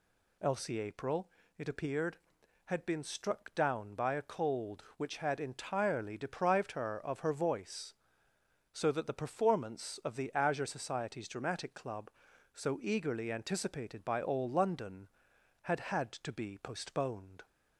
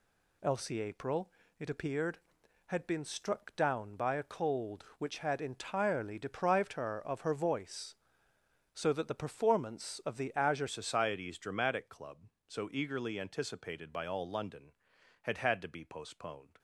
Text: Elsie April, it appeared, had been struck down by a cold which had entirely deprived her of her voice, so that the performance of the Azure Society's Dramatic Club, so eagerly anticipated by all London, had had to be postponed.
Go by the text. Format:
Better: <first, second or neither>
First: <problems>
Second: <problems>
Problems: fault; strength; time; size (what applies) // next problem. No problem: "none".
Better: first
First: none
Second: changes voice at "Society's"; from 10.6 s on; 5.9 s long